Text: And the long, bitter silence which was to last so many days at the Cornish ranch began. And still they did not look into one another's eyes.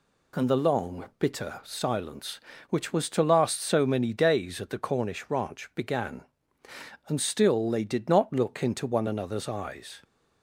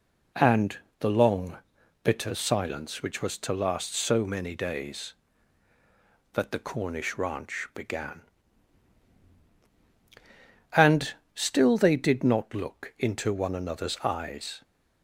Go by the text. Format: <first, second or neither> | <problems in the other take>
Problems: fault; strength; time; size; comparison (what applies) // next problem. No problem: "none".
first | pauses between "And" and "the"; slight; at 0.7 s; 0.24 s long // says "that" for "at"; at 6.3 s // pauses between "And" and "still"; slight; at 11.1 s; 0.22 s long